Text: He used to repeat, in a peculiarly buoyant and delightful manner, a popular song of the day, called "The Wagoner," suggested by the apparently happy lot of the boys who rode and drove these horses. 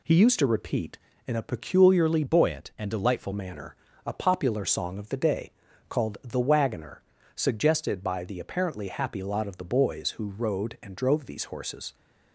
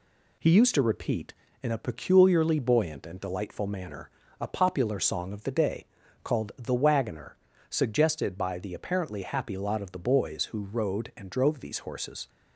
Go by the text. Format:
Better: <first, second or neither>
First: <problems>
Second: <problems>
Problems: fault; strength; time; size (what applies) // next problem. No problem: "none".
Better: second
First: changes voice from "buoyant" to "delightful"; from 2.2 to 3.3 s; 1.1 s long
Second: none